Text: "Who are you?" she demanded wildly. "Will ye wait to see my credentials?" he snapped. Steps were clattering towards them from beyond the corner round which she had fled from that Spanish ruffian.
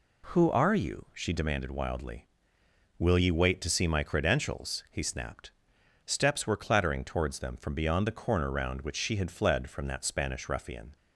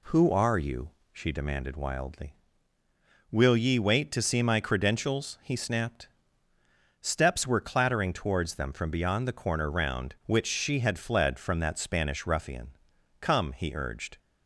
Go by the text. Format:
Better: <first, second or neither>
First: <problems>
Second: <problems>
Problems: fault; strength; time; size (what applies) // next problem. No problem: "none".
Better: first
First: none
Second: goes on to say "Come he urged"; noticeable; from 13.2 s on; 0.96 s long